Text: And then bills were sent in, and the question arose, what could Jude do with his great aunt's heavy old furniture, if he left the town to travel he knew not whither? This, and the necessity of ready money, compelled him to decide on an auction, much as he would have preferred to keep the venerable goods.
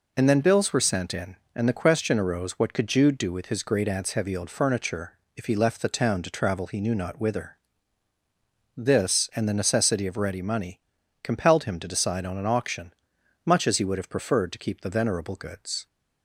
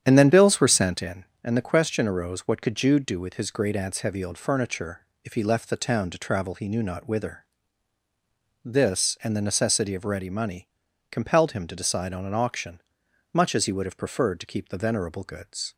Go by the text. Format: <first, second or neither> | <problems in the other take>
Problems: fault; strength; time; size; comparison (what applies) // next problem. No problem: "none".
first | starts louder than the rest; strong; until 1.1 s; 9 dB